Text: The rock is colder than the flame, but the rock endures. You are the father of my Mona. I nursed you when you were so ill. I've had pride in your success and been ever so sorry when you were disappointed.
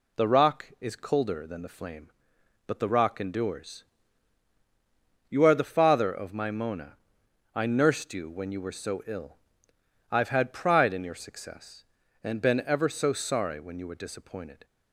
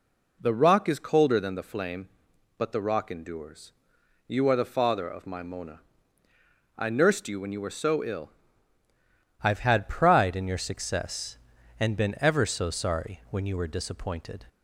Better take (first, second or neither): first